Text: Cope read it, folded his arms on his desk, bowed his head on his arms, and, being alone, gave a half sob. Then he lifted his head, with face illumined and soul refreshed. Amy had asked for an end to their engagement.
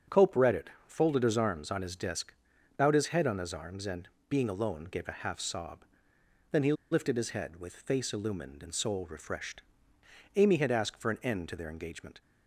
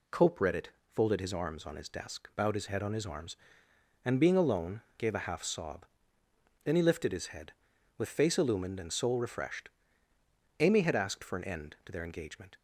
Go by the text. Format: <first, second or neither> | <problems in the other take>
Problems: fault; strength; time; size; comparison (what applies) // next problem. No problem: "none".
second | starts louder than the rest; strong; until 1.2 s; 7 dB // pauses between "he" and "lifted"; slight; at 6.7 s; 0.18 s long